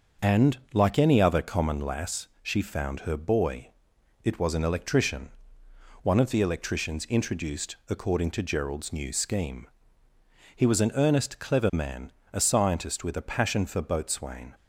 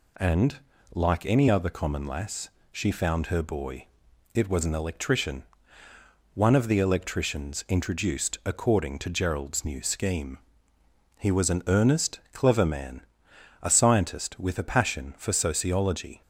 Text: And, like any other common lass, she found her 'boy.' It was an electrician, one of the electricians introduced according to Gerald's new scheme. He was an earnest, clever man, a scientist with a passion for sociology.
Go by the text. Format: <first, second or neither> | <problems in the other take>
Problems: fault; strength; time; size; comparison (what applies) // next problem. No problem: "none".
second | starts louder than the rest; until 1.3 s; 6.5 dB // says "boatswain" for "sociology"; at 13.8 s